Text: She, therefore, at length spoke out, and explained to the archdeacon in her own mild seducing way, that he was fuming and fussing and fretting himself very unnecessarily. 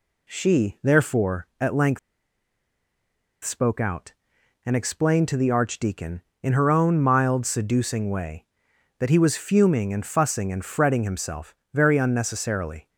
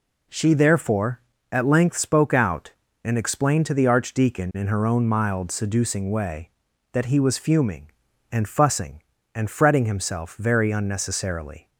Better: second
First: pauses between "length" and "spoke"; strong; at 1.9 s; 1.4 s long // pauses between "himself" and "very"; slight; at 11.5 s; 0.18 s long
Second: none

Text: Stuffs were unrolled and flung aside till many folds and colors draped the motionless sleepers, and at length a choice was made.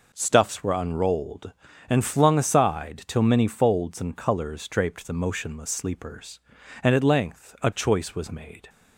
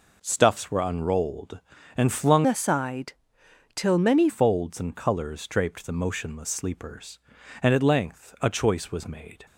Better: first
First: none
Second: changes voice from "aside" to "many"; from 2.4 to 4.2 s; 1.8 s long // pauses between "aside" and "till"; noticeable; at 3.1 s; 0.62 s long

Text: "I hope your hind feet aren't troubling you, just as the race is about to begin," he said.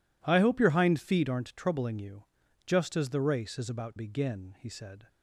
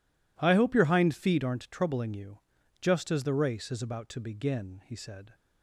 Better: second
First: skips "to"; at 3.9 s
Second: none

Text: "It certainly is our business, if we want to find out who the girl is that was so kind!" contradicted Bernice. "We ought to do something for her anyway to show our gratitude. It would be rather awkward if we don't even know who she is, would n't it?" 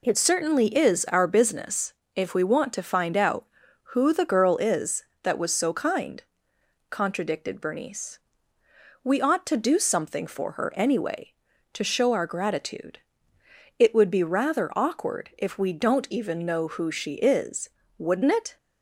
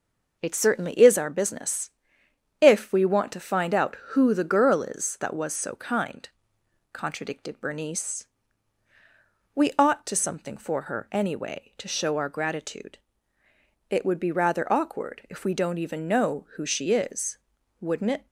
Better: first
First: none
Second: skips "do"; at 10.1 s

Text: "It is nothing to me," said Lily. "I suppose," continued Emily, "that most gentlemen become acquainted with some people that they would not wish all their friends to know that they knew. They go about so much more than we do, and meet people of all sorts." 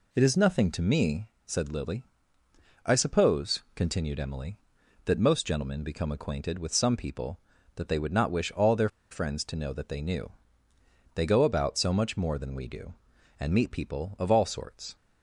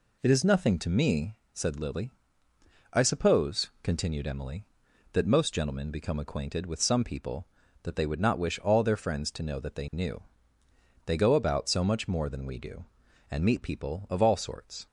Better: second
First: pauses between "their" and "friends"; slight; at 8.8 s; 0.22 s long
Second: none

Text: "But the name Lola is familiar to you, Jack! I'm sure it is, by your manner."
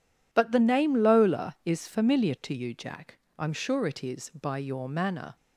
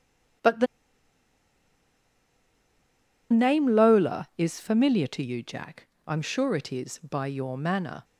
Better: first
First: none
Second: pauses between "the" and "name"; strong; at 0.6 s; 2.6 s long

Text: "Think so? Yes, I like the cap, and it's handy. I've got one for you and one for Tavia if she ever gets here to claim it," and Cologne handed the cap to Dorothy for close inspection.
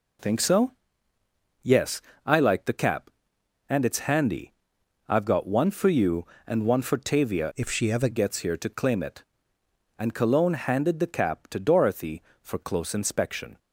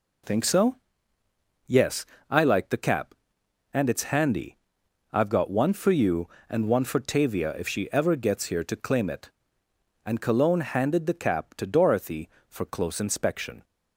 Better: second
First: changes voice from "if" to "ever"; from 7.5 to 8.0 s; 0.5 s long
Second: none

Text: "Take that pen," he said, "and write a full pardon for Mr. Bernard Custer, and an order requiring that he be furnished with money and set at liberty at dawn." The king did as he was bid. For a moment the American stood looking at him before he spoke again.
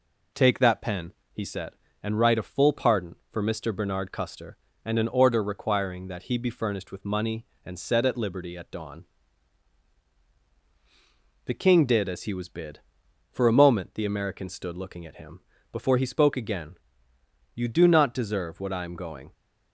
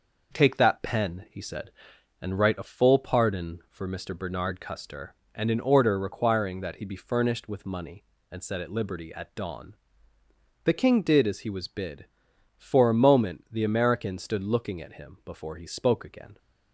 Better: second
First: pauses between "him" and "before"; slight; at 15.4 s; 0.32 s long // goes on to say "You do not deserve what I am going"; strong; from 17.5 s on; 1.7 s long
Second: none

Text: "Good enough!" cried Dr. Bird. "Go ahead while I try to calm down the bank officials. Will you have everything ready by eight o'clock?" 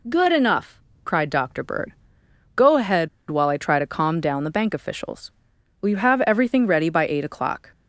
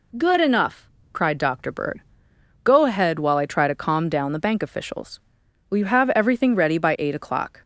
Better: second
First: pauses between "ahead" and "while"; slight; at 3.0 s; 0.22 s long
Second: none

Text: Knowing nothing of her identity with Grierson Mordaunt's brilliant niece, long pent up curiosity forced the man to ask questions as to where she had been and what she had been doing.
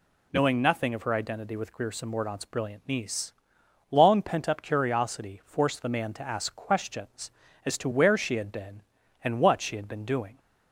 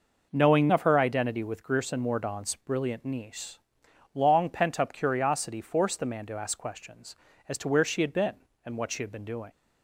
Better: first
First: none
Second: skips "nothing"; at 0.6 s

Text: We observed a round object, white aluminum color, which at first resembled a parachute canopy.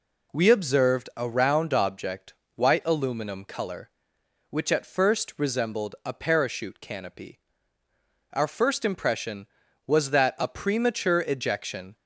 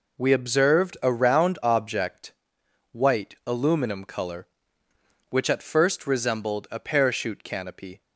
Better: second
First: goes on to say "Our first impression was that a premature ejection"; strong; from 8.3 s on; 3.6 s long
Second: none

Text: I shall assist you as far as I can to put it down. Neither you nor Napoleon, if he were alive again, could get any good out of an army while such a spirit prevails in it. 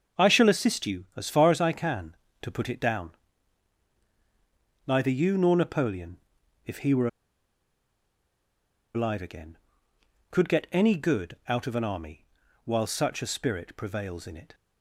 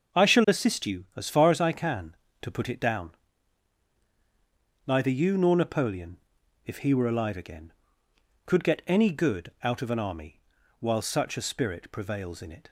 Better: second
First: starts louder than the rest; until 1.2 s; 6.5 dB // pauses between "were" and "alive"; strong; at 7.0 s; 1.8 s long // pauses between "army" and "while"; at 12.2 s; 0.40 s long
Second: starts louder than the rest; until 1.2 s; 6.5 dB // pauses between "army" and "while"; at 10.3 s; 0.40 s long

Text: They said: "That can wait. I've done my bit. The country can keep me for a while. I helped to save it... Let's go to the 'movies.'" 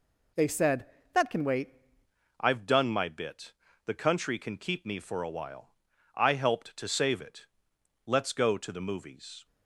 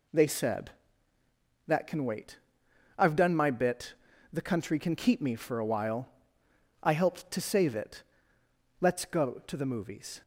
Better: second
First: changes voice at "I've"; from 2.3 s on; 7.1 s long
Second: none

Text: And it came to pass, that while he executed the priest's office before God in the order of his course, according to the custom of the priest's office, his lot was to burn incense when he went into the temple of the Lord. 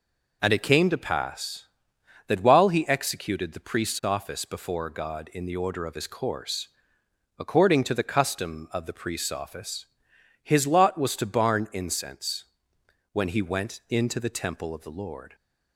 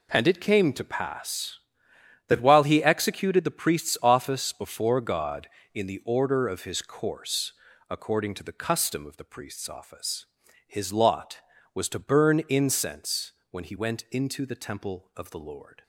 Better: second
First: says "barn" for "burn"; at 11.2 s // pauses between "incense" and "when"; noticeable; at 12.4 s; 0.68 s long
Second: pauses between "incense" and "when"; slight; at 13.3 s; 0.18 s long

